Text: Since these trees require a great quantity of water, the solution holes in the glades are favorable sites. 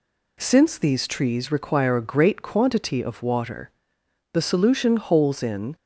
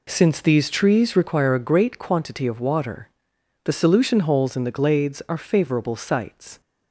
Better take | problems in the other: second | stops before "the glades are favorable sites"; at 5.7 s

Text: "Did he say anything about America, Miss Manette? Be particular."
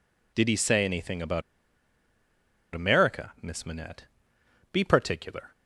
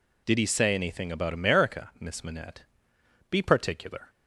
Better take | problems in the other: second | pauses between "about" and "America"; strong; at 1.4 s; 1.3 s long

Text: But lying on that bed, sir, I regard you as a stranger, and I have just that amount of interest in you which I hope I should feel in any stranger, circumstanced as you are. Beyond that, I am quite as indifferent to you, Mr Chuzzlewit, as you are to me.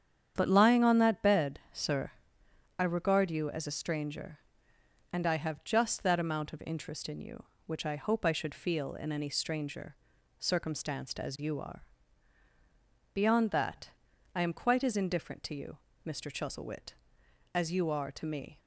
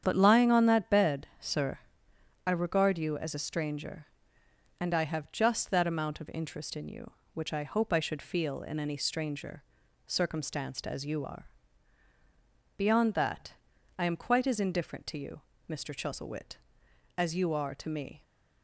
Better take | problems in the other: neither | starts louder than the rest; strong; the same in both

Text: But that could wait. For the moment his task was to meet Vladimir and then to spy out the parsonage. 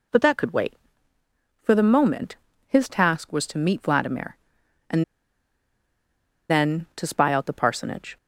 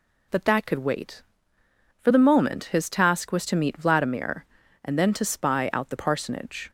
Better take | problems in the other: second | pauses between "moment" and "his"; slight; at 2.3 s; 0.30 s long // pauses between "and" and "then"; strong; at 5.0 s; 1.4 s long

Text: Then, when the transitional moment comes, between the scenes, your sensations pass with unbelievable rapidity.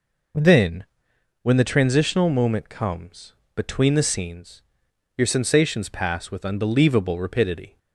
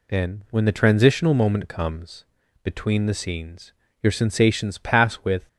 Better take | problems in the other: first | stops before "unbelievable rapidity"; at 5.4 s

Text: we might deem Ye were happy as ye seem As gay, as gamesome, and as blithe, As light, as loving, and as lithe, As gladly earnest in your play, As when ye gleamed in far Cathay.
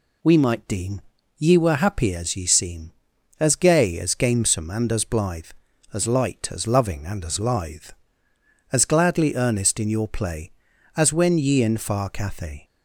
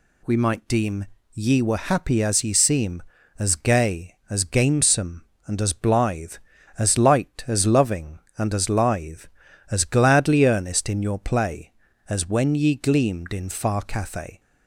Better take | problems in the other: second | pauses between "deem" and "Ye"; slight; at 1.0 s; 0.36 s long; slight in the second // skips "gleamed"; at 11.6 s

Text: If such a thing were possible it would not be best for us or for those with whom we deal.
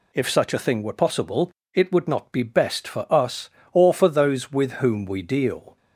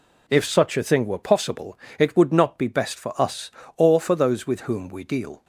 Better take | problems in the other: neither | pauses between "possible" and "it"; slight; the same in both

